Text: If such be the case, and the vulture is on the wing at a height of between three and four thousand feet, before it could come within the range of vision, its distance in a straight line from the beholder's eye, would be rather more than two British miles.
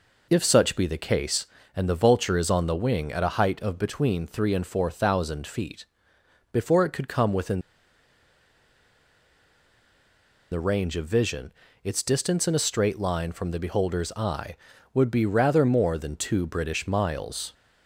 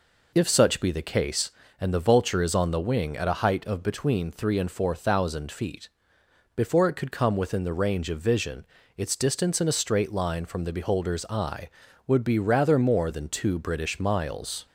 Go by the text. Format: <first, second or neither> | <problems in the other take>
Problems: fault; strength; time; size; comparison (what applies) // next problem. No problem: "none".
second | pauses between "within" and "the"; strong; at 7.6 s; 2.9 s long